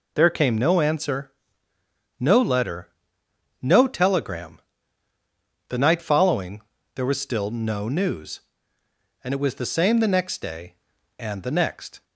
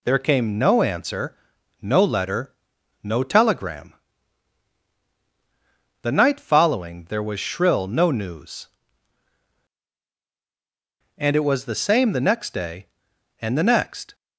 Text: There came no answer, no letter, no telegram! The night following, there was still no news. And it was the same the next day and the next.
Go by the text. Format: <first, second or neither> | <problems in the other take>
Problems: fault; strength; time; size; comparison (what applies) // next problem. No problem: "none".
first | says "shrill" for "still"; at 7.3 s